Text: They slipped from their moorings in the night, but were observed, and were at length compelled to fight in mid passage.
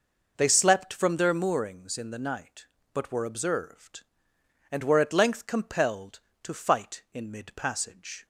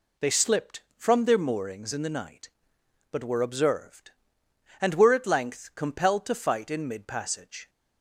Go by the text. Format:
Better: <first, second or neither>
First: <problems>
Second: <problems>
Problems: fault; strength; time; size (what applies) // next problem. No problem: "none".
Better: second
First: says "slept" for "slipped"; at 0.4 s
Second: none